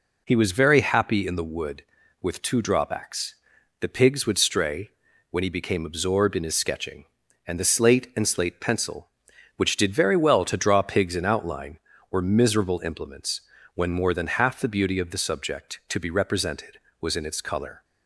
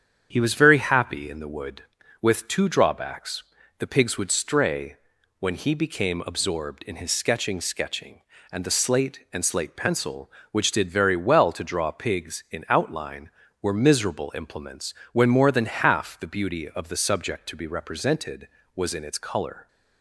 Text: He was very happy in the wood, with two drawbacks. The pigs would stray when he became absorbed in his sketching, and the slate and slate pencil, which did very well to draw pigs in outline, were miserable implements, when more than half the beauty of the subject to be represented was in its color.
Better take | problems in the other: first | starts louder than the rest; strong; until 1.3 s; 8.5 dB // pauses between "stray" and "when"; at 4.9 s; 0.44 s long; also in the first // says "sketching" twice; at 7.5 s

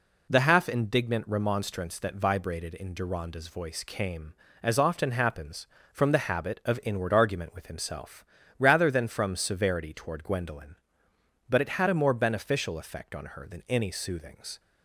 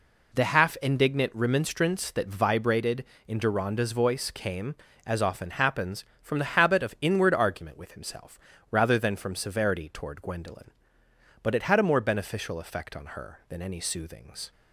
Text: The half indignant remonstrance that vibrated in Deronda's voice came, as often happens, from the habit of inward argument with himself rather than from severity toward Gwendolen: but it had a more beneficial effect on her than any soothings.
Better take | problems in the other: neither | pauses between "himself" and "rather"; slight; the same in both

